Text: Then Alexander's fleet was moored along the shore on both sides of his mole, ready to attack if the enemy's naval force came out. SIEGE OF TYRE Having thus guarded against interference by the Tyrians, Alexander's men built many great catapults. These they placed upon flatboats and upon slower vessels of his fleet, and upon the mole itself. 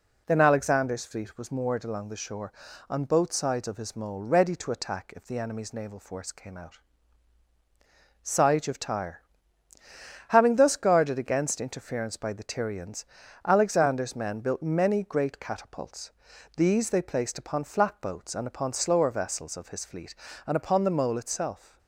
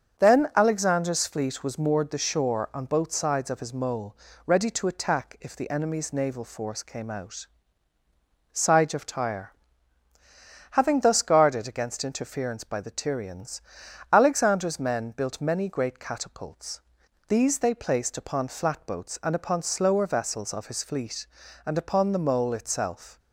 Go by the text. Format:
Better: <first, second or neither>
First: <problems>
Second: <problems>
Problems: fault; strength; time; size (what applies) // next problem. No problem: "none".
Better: first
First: pauses between "TYRE" and "Having"; at 9.2 s; 1.0 s long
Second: starts louder than the rest; until 1.2 s; 6.5 dB // skips "along"; at 2.1 s // pauses between "TYRE" and "Having"; at 9.5 s; 1.1 s long